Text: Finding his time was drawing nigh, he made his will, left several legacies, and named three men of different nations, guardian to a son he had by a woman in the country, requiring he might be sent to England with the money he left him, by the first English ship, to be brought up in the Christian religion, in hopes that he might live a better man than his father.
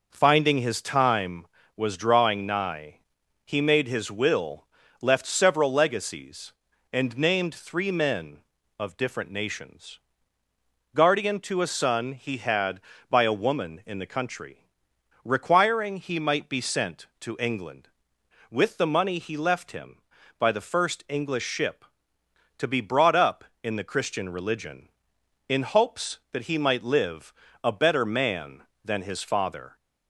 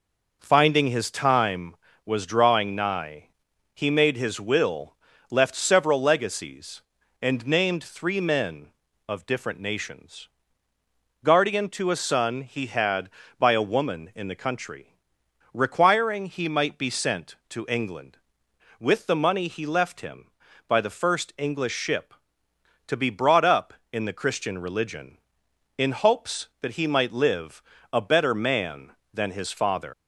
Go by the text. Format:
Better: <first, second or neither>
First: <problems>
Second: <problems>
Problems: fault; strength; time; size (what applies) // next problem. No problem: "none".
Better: first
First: pauses between "live" and "a"; slight; at 27.3 s; 0.32 s long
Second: pauses between "live" and "a"; slight; at 27.6 s; 0.32 s long // leaves "father" unfinished; at 29.9 s; 110 ms